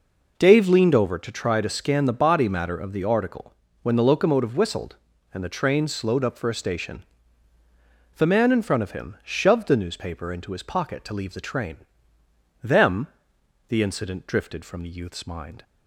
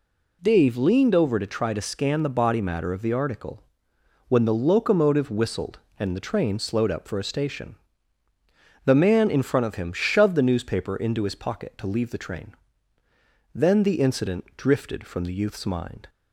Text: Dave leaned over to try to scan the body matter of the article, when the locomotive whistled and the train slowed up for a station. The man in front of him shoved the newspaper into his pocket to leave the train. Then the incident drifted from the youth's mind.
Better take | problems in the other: second | says "Them" for "Then"; at 12.6 s

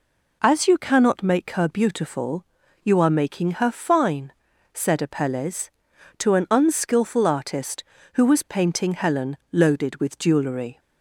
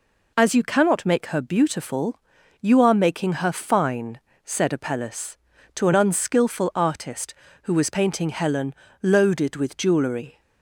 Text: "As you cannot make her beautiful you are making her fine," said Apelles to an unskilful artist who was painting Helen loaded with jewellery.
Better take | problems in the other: neither | pauses between "beautiful" and "you"; the same in both // pauses between "Helen" and "loaded"; slight; the same in both

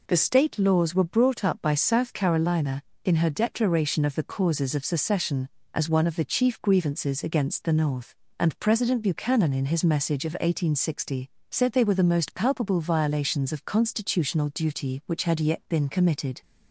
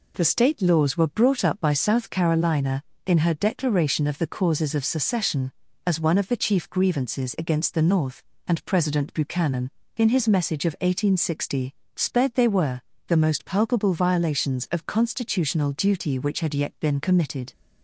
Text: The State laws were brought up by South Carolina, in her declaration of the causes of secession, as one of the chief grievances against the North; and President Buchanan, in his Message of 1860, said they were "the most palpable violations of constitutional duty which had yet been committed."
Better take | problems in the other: first | says "sped" for "said"; at 11.9 s // pauses between "were" and "the"; slight; at 12.7 s; 0.28 s long

